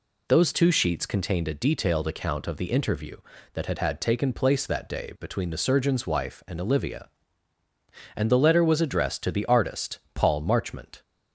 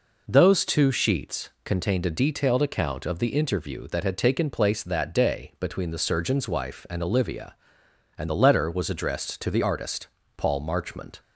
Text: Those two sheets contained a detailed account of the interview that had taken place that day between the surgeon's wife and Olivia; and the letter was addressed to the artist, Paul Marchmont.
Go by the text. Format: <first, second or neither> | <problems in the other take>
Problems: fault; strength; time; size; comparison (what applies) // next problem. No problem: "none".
second | says "had" twice; at 3.7 s